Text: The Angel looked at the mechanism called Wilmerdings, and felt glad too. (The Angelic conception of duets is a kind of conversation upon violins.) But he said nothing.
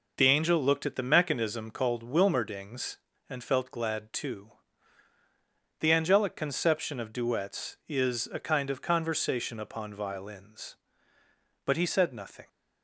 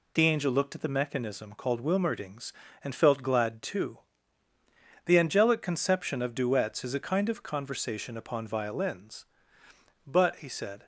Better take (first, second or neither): first